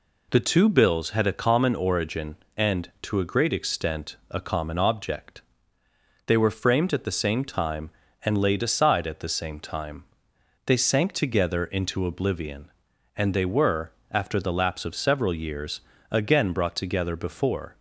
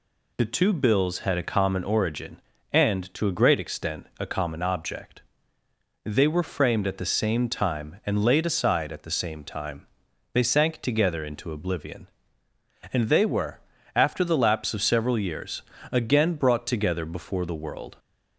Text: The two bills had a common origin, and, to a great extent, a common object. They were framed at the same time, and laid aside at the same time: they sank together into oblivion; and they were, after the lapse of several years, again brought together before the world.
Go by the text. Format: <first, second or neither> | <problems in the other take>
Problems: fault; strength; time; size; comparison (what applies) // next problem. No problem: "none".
second | stops before "the world"; at 17.7 s